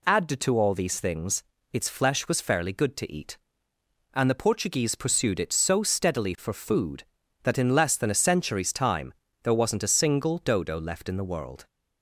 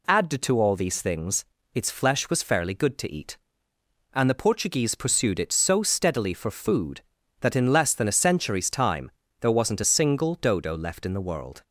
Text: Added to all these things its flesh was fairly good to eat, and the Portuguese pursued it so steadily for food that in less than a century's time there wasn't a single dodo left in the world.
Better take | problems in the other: neither | pauses between "things" and "its"; slight; the same in both // pauses between "time" and "there"; slight; the same in both

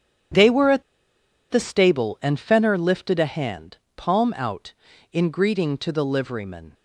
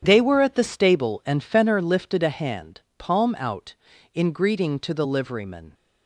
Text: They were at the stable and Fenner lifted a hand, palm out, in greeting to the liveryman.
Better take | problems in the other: second | starts louder than the rest; strong; until 2.0 s; 9 dB; strong in the second // pauses between "at" and "the"; noticeable; at 0.8 s; 0.69 s long

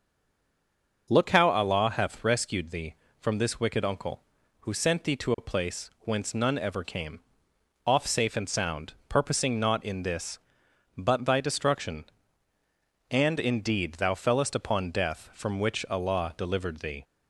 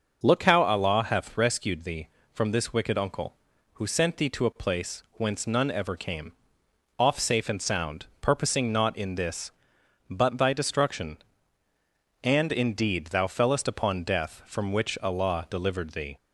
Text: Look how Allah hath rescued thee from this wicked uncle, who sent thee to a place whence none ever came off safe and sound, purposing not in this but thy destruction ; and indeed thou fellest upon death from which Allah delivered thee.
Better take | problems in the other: second | stays silent before the first word; until 1.0 s; 1.0 s long // pauses between "came" and "off"; noticeable; at 7.1 s; 0.66 s long; noticeable in the second

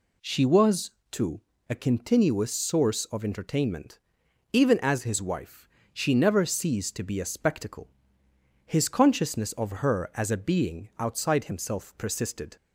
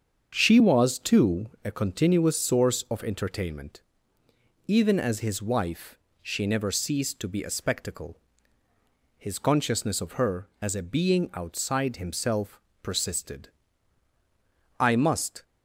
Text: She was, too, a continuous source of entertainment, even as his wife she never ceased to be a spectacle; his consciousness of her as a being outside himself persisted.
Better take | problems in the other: first | starts louder than the rest; until 1.3 s; 7 dB // pauses between "wife" and "she"; slight; at 5.9 s; 0.24 s long; slight in the first // pauses between "himself" and "persisted"; slight; at 12.5 s; 0.22 s long // goes on to say "I must"; noticeable; from 14.7 s on; 0.64 s long

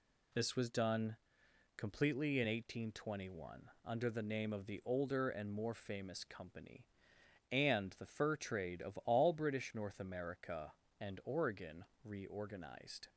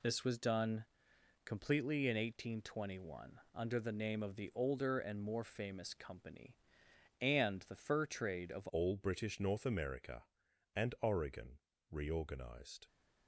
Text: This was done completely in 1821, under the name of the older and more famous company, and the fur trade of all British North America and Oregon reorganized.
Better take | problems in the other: first | pauses between "done" and "completely"; noticeable; at 0.8 s; 0.60 s long; noticeable in the first // changes voice at "all"; from 8.7 s on; 4.1 s long // pauses between "Oregon" and "reorganized"; slight; at 11.5 s; 0.32 s long; slight in the first

